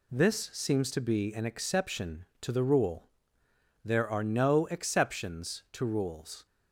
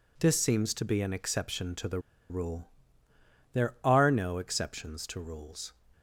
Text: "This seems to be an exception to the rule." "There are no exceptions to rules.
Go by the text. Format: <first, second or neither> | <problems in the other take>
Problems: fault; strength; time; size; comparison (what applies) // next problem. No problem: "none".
first | pauses between "the" and "rule"; slight; at 1.9 s; 0.31 s long